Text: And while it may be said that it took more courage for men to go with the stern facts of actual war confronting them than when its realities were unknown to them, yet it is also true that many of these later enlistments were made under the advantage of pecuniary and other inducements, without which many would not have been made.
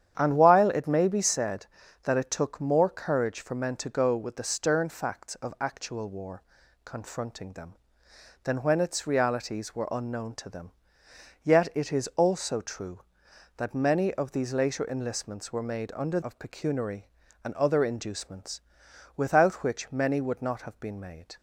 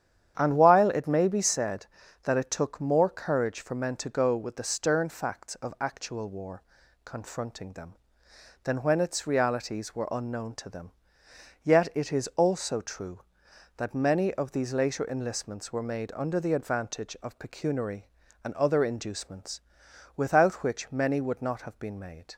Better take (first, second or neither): second